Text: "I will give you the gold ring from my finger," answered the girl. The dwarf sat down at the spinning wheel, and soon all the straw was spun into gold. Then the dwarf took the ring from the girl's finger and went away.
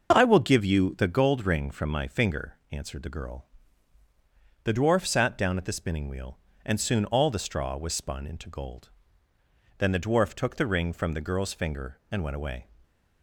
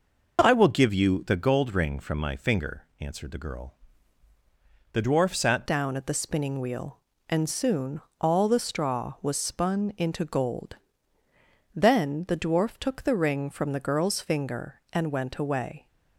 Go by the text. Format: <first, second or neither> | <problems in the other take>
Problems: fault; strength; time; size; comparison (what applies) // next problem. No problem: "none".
first | changes voice at "down"; from 5.6 s on; 10.2 s long // pauses between "soon" and "all"; slight; at 8.0 s; 0.20 s long